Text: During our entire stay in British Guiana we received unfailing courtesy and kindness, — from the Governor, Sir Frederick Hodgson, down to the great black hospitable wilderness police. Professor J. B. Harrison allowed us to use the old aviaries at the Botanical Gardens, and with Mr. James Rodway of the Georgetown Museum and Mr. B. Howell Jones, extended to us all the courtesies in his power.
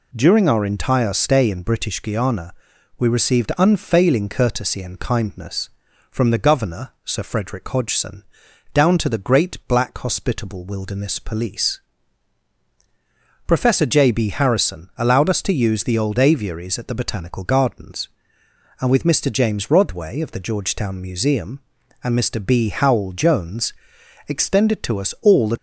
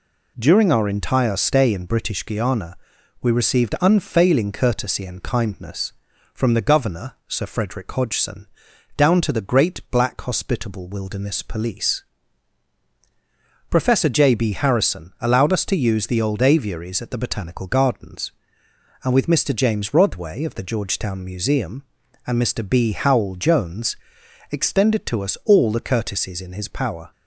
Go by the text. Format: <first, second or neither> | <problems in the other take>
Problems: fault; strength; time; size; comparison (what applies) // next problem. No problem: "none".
second | pauses between "Guiana" and "we"; noticeable; at 2.5 s; 0.46 s long; noticeable in the second // stops before "courtesies in his power"; at 25.5 s